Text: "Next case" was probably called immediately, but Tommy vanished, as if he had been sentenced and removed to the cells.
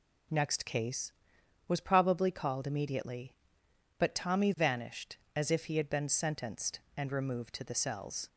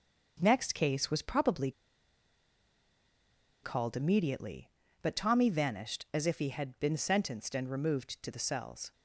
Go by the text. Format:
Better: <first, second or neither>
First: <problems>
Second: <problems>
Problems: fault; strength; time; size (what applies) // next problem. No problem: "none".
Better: first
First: none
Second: starts louder than the rest; until 1.4 s; 6.5 dB // pauses between "probably" and "called"; strong; at 1.7 s; 1.9 s long